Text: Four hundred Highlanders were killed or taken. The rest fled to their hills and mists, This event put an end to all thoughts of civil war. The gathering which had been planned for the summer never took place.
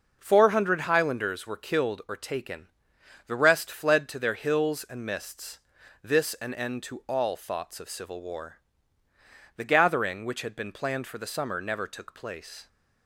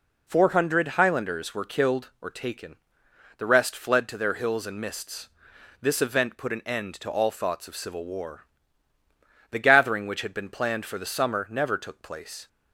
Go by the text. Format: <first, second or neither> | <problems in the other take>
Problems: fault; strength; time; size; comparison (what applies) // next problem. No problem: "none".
second | skips "event put"; at 6.3 s